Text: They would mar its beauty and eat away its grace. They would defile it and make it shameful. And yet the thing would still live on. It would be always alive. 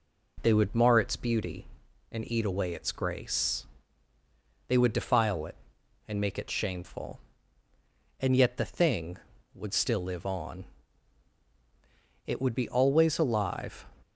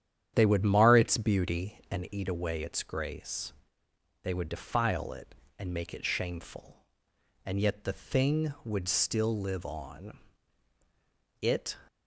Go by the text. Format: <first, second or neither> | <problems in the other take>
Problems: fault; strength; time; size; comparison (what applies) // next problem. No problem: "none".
first | starts louder than the rest; strong; until 1.3 s; 9.5 dB // stops before "would be always alive"; at 11.8 s